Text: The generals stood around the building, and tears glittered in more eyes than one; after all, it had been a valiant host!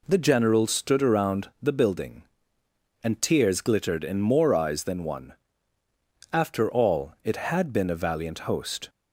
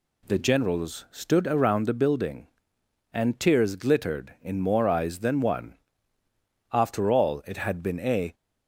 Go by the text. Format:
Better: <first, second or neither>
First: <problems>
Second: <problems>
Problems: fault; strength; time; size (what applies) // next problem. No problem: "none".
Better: first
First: none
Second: stops before "valiant host"; at 8.3 s